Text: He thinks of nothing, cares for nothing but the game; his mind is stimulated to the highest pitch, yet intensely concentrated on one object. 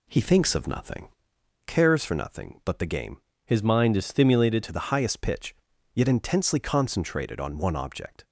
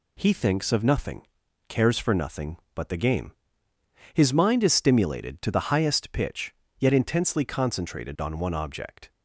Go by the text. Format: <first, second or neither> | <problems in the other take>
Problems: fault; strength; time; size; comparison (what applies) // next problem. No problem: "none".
second | changes voice from "his" to "stimulated"; from 3.4 to 4.6 s; 1.2 s long